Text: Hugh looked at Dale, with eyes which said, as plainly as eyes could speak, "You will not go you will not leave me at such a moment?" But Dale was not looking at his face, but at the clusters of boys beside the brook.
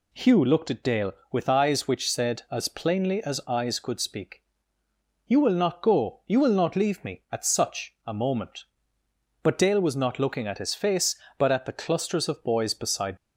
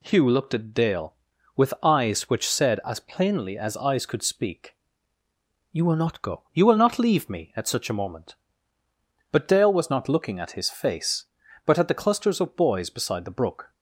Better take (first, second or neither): second